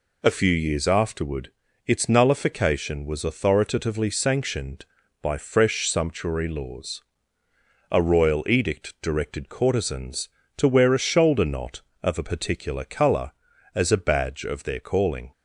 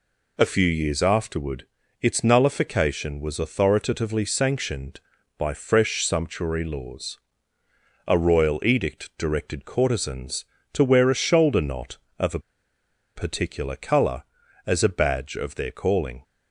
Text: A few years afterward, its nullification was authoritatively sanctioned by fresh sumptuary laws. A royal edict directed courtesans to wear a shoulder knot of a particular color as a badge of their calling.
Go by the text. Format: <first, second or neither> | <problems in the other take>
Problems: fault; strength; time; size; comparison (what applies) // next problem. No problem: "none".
first | pauses between "a" and "particular"; noticeable; at 12.3 s; 0.77 s long